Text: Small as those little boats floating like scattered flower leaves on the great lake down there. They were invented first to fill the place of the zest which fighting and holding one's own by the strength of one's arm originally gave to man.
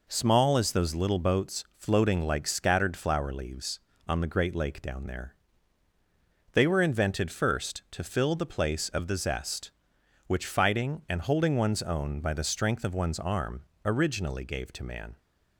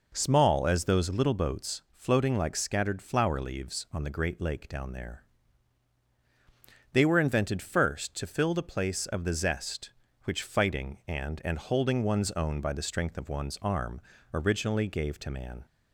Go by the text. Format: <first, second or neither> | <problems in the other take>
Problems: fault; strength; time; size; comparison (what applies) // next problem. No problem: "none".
first | says "and" twice; at 11.4 s // pauses between "arm" and "originally"; slight; at 14.0 s; 0.34 s long; slight in the first